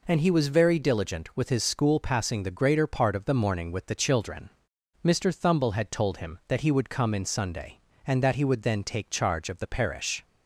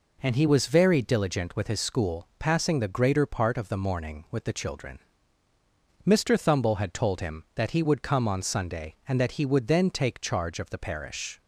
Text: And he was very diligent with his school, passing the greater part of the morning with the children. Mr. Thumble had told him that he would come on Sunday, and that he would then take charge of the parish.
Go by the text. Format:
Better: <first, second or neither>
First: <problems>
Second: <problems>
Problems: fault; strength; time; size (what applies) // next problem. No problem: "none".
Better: second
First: says "in" for "on"; at 7.1 s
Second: none